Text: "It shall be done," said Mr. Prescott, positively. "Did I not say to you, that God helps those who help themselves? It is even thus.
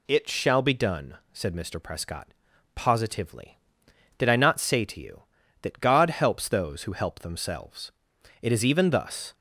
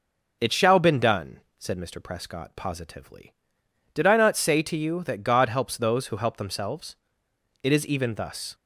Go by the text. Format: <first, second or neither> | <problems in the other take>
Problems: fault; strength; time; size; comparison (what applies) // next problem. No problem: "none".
first | says "been" for "be"; at 0.7 s